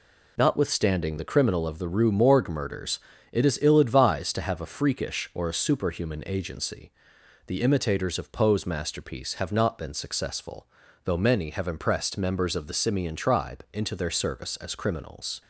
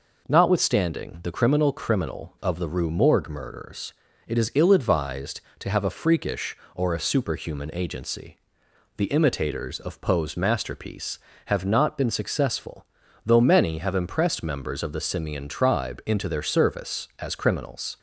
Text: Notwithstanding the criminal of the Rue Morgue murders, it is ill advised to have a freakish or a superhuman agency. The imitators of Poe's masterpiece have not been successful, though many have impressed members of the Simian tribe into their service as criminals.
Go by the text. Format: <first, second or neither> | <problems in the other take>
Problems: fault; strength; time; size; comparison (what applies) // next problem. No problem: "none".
first | says "criminal" twice; at 1.7 s